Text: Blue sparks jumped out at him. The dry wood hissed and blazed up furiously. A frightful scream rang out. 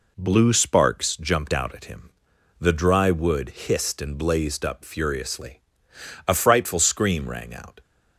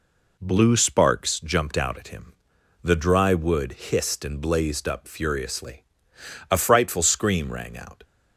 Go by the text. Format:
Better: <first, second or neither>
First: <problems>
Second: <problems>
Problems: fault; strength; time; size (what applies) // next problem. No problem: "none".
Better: neither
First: none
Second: none